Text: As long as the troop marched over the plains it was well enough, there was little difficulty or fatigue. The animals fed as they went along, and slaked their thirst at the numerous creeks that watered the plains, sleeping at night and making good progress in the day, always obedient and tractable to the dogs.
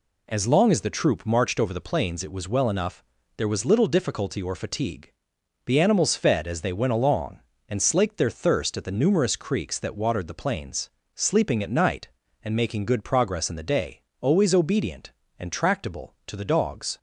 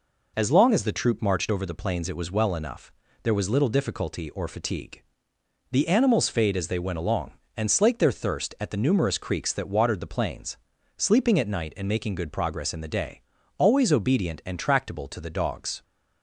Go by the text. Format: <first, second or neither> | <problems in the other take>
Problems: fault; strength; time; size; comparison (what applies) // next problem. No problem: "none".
first | says "fade" for "fed"; at 6.2 s